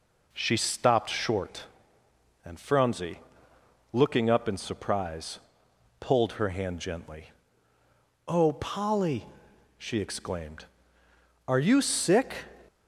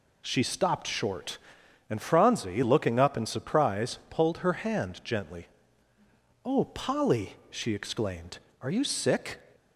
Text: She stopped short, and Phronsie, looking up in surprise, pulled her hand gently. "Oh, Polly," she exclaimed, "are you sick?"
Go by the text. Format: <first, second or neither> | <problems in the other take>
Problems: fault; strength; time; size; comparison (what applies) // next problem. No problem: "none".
neither | none